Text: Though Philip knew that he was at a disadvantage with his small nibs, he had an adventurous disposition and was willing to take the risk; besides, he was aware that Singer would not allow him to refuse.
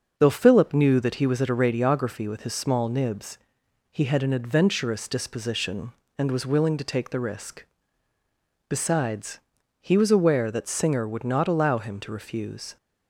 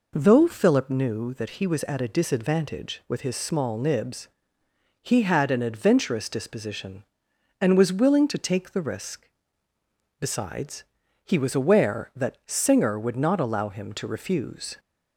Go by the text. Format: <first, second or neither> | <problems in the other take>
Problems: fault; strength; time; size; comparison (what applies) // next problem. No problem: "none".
second | starts louder than the rest; until 1.1 s; 6.5 dB // says "radiography" for "disadvantage"; at 1.5 s